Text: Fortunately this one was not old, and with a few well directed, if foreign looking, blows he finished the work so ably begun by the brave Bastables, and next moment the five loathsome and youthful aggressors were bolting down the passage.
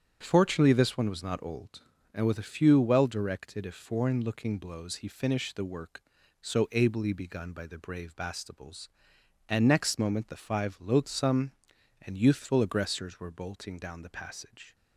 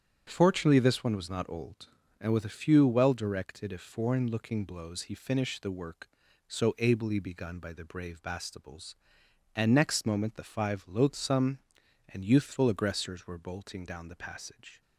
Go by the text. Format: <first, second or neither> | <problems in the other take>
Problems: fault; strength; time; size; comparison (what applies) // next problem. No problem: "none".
neither | starts louder than the rest; strong; the same in both